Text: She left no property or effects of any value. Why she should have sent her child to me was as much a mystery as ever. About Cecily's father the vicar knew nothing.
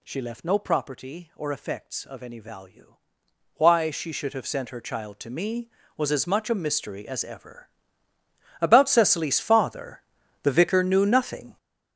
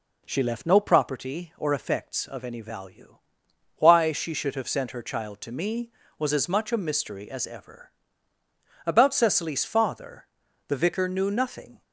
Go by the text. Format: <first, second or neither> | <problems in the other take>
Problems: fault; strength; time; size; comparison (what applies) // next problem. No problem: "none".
second | gets louder; strong; throughout; 11 dB // pauses between "father" and "the"; at 10.0 s; 0.42 s long; also in the second